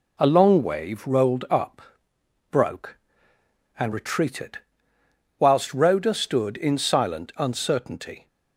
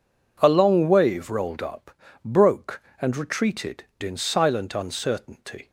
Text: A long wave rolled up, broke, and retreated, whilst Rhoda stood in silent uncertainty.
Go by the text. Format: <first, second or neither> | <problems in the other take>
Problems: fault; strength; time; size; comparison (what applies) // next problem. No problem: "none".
first | skips "whilst Rhoda stood"; at 3.9 s